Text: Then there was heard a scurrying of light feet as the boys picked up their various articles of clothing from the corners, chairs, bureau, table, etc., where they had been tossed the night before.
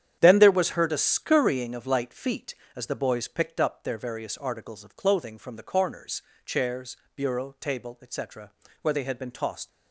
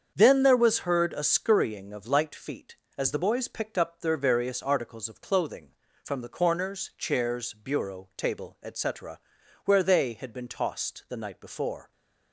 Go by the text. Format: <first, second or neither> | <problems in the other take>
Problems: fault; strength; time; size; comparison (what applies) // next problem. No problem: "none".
second | starts louder than the rest; strong; until 1.2 s; 9 dB; strong in the second // stops before "the night before"; at 9.6 s